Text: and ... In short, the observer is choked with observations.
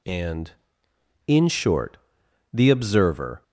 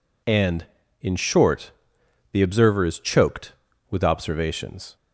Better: second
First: stops before "is choked with observations"; at 3.4 s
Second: none

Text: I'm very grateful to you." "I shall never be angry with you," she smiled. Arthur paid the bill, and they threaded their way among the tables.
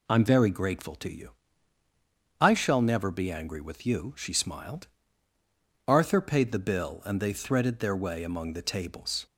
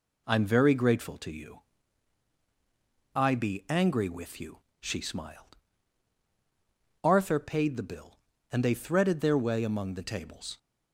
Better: first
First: none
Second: skips "shall never"; at 3.3 s

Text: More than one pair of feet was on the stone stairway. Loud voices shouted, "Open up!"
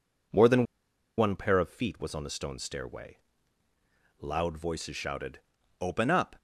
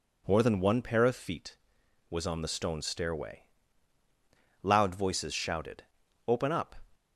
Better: second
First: pauses between "than" and "one"; noticeable; at 0.6 s; 0.55 s long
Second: none

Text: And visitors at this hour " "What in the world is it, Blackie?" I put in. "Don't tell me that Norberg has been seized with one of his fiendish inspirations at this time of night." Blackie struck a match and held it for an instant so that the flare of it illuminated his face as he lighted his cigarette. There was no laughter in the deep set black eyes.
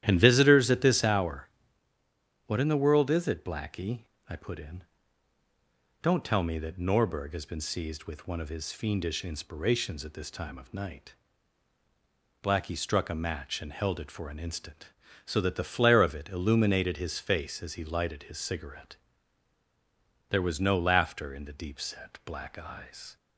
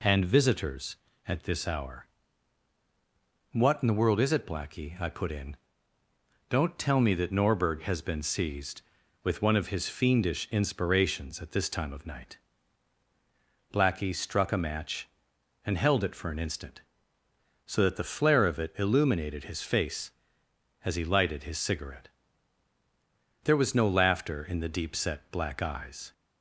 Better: second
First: starts louder than the rest; strong; until 1.2 s; 11.5 dB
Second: none

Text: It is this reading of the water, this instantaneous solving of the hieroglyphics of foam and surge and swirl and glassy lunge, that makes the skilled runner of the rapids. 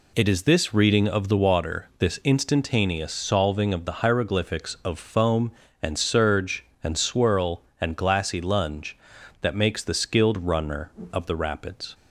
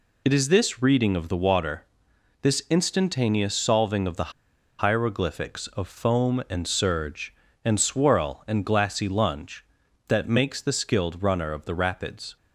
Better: first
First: none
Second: pauses between "the" and "hieroglyphics"; noticeable; at 4.3 s; 0.49 s long

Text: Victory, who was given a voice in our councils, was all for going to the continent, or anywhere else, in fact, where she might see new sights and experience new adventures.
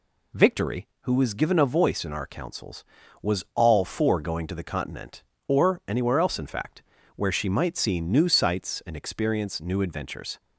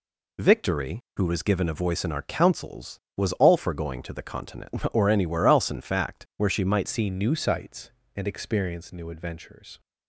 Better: first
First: none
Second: changes voice at "see"; from 6.8 s on; 2.9 s long

